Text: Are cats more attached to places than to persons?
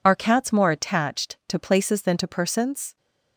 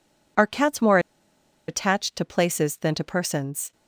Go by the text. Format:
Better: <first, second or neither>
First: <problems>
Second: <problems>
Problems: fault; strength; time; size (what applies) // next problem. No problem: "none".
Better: first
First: none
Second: pauses between "more" and "attached"; noticeable; at 0.9 s; 0.69 s long